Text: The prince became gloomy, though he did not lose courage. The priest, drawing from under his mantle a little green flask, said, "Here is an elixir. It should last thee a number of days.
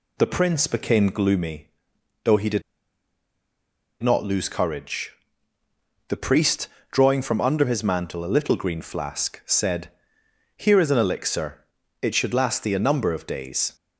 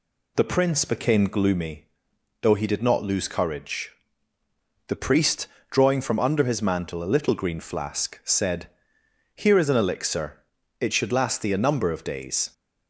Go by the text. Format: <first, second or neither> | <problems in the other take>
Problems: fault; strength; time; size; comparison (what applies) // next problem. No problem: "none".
second | pauses between "did" and "not"; strong; at 2.6 s; 1.4 s long